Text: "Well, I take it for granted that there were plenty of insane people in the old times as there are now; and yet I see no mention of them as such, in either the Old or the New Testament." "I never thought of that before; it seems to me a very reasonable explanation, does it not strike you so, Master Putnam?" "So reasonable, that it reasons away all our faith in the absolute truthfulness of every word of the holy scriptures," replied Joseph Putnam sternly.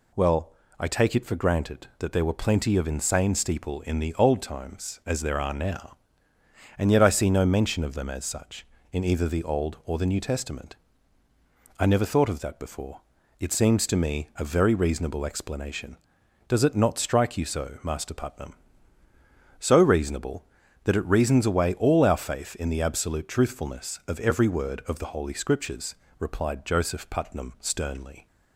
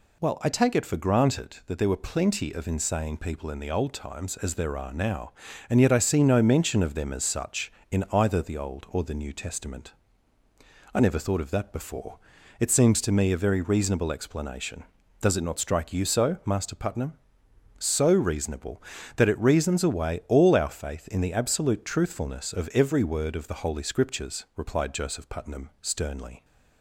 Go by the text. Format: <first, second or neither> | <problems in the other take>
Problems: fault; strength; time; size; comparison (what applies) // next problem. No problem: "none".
second | says "steeple" for "people"; at 3.3 s